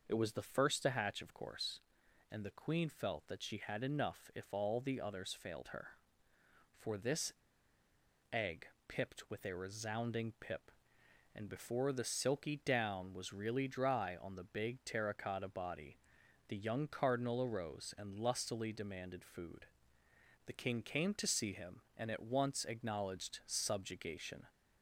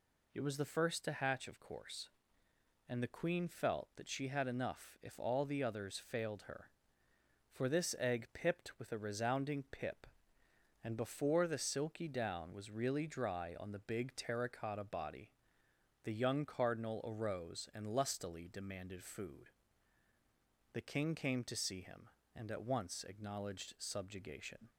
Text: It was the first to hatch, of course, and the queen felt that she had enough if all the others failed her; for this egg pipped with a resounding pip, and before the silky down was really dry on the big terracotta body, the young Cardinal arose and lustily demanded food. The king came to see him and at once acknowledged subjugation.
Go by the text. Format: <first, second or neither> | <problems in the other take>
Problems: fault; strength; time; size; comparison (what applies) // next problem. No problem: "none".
second | pauses between "this" and "egg"; at 7.3 s; 0.98 s long // pauses between "egg" and "pipped"; slight; at 8.6 s; 0.18 s long